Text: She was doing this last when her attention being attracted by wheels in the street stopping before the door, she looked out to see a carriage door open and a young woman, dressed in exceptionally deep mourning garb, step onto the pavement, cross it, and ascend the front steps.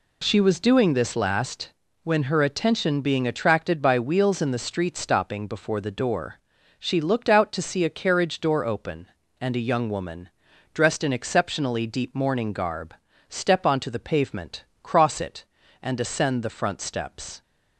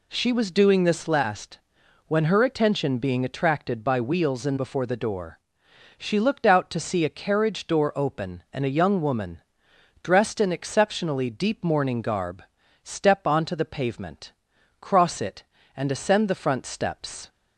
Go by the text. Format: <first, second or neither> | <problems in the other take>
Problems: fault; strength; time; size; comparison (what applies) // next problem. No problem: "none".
first | pauses between "last" and "when"; noticeable; at 1.5 s; 0.50 s long; slight in the first // skips "the street stopping"; at 4.5 s